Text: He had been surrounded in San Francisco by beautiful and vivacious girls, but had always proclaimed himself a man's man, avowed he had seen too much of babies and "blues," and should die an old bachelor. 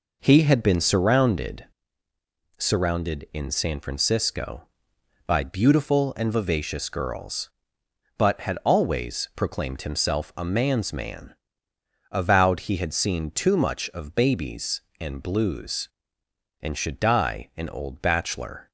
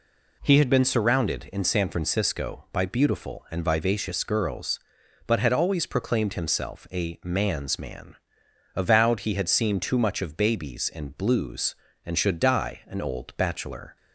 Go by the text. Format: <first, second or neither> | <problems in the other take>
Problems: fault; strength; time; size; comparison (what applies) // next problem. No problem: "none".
second | says "surrounded" twice; at 2.5 s